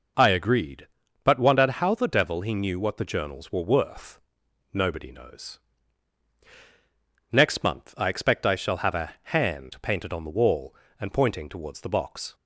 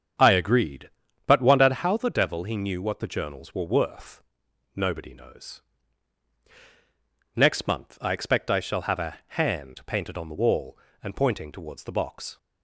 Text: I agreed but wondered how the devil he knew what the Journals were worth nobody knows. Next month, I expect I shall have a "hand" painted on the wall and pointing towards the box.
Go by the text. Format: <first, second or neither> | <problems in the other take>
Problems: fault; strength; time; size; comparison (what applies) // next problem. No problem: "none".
first | starts louder than the rest; strong; until 2.0 s; 7.5 dB // pauses between "worth" and "nobody"; noticeable; at 4.2 s; 0.52 s long; noticeable in the first